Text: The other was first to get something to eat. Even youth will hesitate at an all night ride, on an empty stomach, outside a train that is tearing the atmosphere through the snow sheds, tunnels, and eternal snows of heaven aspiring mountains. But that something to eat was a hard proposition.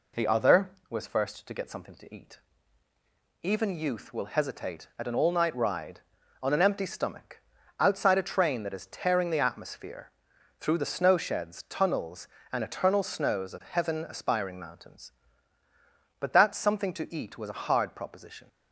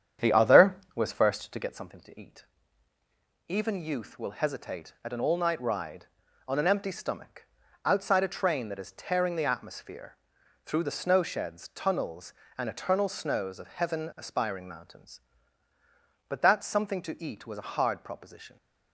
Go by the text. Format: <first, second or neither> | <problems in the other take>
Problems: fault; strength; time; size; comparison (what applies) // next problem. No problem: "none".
first | starts louder than the rest; strong; until 1.8 s; 8.5 dB // pauses between "atmosphere" and "through"; noticeable; at 10.1 s; 0.50 s long; noticeable in the first